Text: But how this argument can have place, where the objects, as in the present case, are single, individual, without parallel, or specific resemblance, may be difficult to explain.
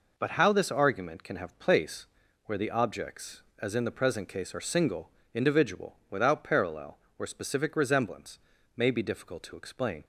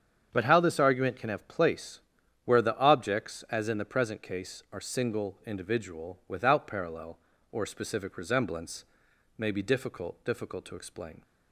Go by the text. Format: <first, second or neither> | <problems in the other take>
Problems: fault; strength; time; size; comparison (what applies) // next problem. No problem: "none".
first | starts louder than the rest; strong; until 1.3 s; 7.5 dB // says "difficult" twice; at 10.2 s